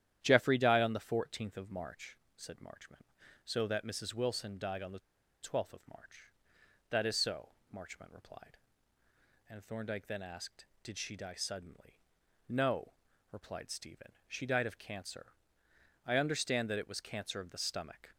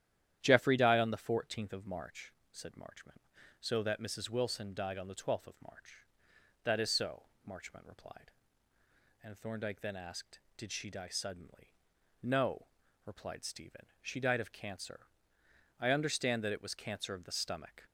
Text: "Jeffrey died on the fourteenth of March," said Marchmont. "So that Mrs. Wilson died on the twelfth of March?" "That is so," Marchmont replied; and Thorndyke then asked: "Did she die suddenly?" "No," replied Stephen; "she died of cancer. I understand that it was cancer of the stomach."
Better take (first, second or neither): second